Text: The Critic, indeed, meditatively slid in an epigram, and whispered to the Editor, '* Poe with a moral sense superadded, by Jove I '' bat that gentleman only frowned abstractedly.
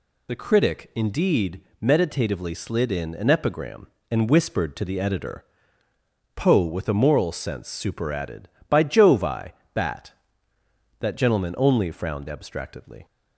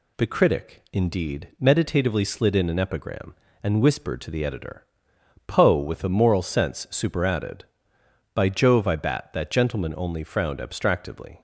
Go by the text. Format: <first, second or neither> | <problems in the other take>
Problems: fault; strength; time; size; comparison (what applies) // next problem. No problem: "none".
second | loses the start of "The"; at 0.2 s; 25 ms